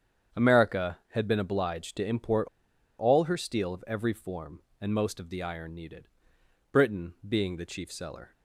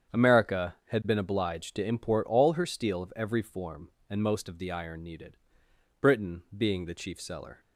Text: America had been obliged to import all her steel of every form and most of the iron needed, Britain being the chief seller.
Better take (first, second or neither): second